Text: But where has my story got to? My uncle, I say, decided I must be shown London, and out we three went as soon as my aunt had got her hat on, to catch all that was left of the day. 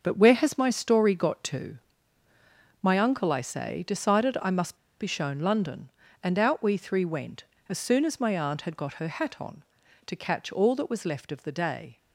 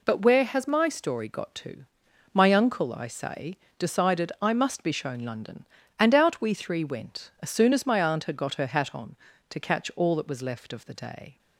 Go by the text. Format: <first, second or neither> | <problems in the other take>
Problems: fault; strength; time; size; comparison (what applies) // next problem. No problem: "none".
second | starts louder than the rest; until 1.0 s; 6.5 dB // pauses between "must" and "be"; slight; at 4.7 s; 0.24 s long